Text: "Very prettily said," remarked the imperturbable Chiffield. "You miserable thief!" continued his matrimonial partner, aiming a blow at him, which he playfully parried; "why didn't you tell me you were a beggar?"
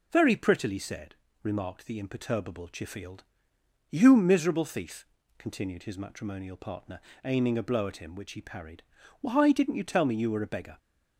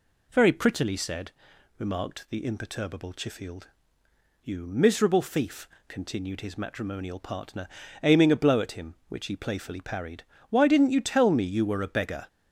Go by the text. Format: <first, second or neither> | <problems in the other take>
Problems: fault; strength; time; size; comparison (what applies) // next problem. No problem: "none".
second | skips "playfully"; at 8.4 s